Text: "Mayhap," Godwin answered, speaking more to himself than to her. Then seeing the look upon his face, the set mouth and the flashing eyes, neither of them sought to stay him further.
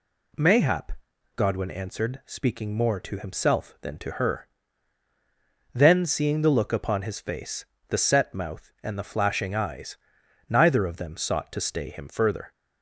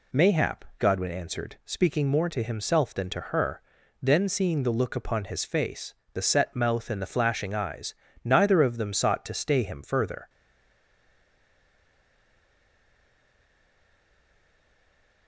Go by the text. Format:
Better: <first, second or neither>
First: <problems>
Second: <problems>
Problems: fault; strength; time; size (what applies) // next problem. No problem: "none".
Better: first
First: none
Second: stays silent after the last word; strong; from 10.2 s on; 5.0 s long